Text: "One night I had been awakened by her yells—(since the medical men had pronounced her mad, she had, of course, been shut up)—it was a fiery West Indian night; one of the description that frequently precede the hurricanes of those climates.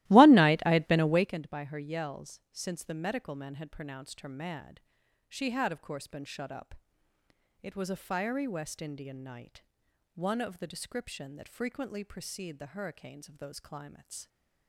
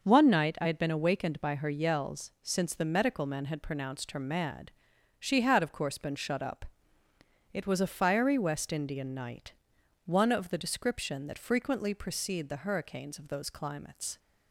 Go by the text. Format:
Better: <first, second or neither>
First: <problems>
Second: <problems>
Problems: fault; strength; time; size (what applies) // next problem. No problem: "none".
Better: second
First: starts louder than the rest; strong; until 1.4 s; 16.5 dB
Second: none